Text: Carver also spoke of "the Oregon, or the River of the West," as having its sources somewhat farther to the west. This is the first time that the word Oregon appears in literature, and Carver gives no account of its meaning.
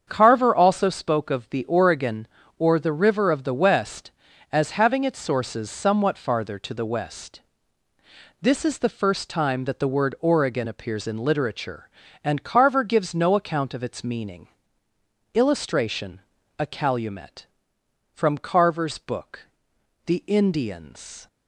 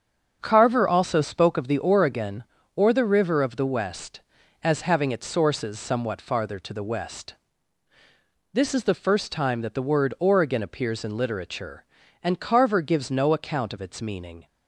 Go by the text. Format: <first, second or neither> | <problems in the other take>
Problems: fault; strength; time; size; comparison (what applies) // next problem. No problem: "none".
second | starts louder than the rest; strong; until 1.0 s; 7.5 dB; also in the second // goes on to say "Illustration A Calumet From Carver's Book The Indians"; strong; from 15.3 s on; 5.9 s long